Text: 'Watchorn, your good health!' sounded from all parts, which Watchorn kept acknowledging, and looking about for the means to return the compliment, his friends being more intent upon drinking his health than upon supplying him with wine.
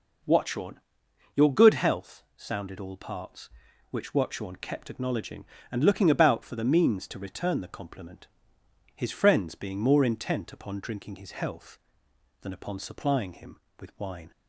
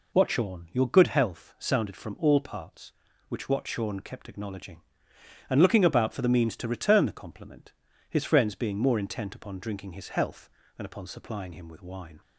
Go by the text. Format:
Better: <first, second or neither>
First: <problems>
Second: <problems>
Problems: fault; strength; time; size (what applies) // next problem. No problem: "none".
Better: second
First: skips "from"; at 2.7 s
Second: none